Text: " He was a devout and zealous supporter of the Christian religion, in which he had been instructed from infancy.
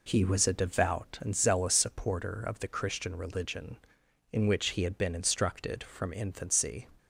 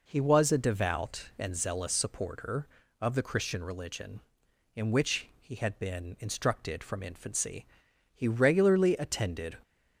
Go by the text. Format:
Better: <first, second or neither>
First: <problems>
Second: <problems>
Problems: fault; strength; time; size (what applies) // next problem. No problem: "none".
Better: first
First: none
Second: goes on to say "He regularly attended"; from 8.1 s on; 1.4 s long